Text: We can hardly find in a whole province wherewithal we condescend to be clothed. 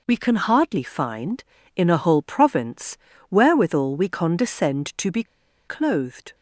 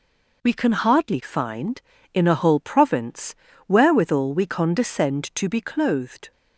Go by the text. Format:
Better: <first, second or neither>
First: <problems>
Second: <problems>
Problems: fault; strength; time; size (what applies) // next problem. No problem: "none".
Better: second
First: pauses between "province" and "wherewithal"; slight; at 2.9 s; 0.32 s long // pauses between "be" and "clothed"; at 5.2 s; 0.44 s long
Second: pauses between "province" and "wherewithal"; slight; at 3.3 s; 0.32 s long